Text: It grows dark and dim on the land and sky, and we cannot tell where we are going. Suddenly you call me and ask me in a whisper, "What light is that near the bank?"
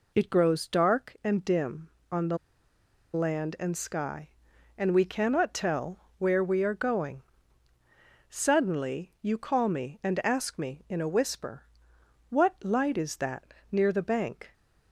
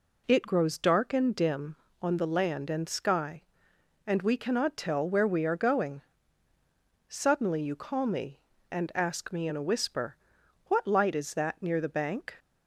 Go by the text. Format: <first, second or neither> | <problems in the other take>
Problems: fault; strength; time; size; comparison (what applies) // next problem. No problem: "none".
second | pauses between "the" and "land"; noticeable; at 2.3 s; 0.76 s long // pauses between "tell" and "where"; slight; at 5.9 s; 0.20 s long // pauses between "that" and "near"; slight; at 13.5 s; 0.20 s long